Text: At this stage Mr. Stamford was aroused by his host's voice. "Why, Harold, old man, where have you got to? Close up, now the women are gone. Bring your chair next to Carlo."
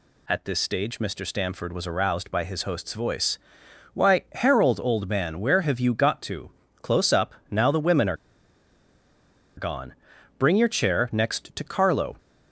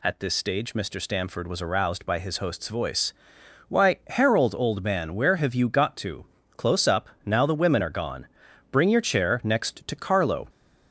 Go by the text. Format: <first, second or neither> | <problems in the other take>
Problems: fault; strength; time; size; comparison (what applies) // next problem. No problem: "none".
second | pauses between "are" and "gone"; strong; at 8.1 s; 1.4 s long